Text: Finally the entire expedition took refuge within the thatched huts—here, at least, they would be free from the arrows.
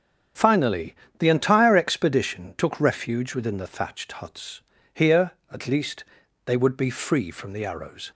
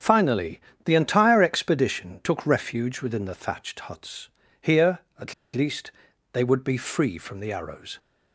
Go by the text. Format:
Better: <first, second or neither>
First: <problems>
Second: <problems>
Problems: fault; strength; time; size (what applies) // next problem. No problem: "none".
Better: first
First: starts louder than the rest; strong; until 1.6 s; 7.5 dB // pauses between "Finally" and "the"; slight; at 0.9 s; 0.25 s long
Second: starts louder than the rest; strong; until 1.2 s; 7.5 dB // pauses between "Finally" and "the"; slight; at 0.5 s; 0.26 s long // pauses between "at" and "least"; slight; at 5.3 s; 0.21 s long